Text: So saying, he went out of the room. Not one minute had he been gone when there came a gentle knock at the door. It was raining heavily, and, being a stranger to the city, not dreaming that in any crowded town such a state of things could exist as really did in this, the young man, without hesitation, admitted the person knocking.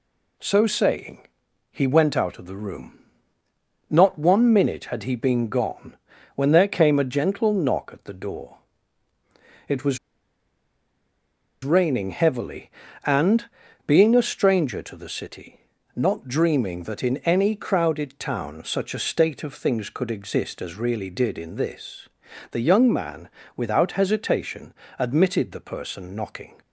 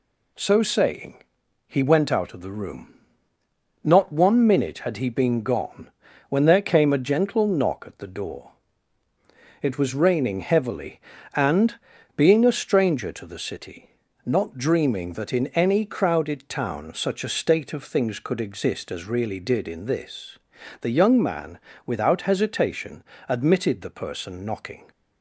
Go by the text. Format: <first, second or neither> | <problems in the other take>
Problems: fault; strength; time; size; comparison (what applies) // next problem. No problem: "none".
second | pauses between "gone" and "when"; at 5.9 s; 0.38 s long; also in the second // pauses between "was" and "raining"; strong; at 9.9 s; 1.6 s long